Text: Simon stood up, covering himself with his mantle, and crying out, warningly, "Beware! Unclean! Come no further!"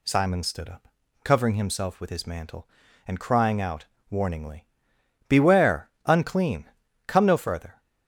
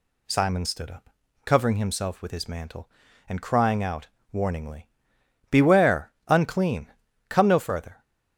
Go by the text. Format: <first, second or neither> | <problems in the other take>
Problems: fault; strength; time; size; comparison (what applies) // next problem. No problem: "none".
neither | none